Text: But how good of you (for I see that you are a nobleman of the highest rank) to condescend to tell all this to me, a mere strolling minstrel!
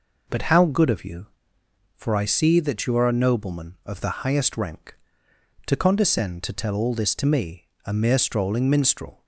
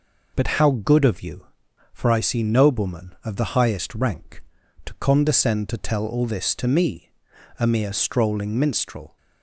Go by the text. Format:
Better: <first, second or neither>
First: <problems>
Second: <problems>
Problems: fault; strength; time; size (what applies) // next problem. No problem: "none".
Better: first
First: none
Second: skips "that you are a"; at 2.4 s